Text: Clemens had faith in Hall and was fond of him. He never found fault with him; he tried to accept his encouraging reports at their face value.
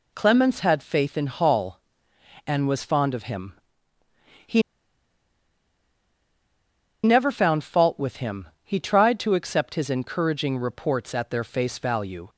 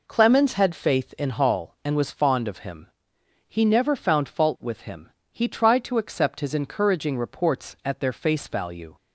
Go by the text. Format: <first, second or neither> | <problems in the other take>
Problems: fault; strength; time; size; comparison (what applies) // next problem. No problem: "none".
second | pauses between "He" and "never"; strong; at 4.6 s; 2.4 s long